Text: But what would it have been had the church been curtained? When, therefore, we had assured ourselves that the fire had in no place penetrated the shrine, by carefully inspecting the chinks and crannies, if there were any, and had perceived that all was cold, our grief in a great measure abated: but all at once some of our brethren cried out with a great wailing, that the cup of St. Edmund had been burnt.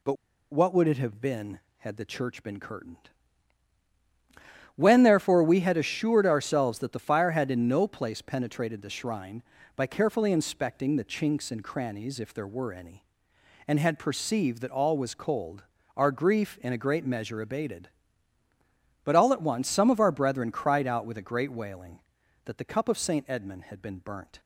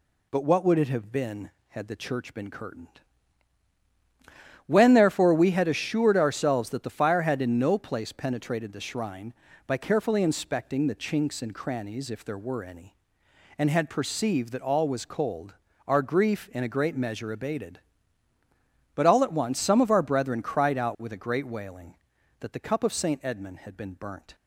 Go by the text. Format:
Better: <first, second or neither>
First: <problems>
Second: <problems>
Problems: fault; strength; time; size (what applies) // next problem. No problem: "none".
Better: second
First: pauses between "But" and "what"; at 0.1 s; 0.38 s long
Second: none